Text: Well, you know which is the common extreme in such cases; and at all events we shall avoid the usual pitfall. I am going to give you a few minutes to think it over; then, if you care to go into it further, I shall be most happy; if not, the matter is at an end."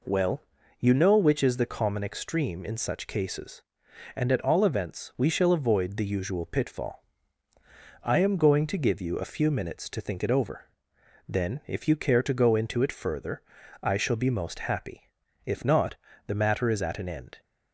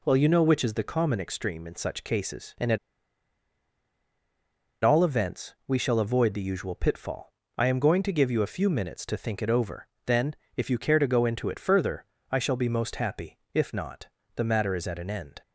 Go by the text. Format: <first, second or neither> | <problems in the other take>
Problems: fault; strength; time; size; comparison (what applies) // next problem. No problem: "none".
first | pauses between "at" and "all"; strong; at 2.7 s; 2.0 s long